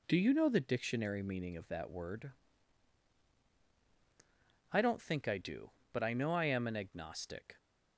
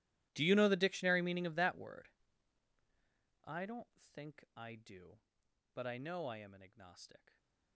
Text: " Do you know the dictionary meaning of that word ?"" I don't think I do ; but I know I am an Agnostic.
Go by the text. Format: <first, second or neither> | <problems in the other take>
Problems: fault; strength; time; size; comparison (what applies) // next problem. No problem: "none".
first | gets quieter; strong; throughout; 17.5 dB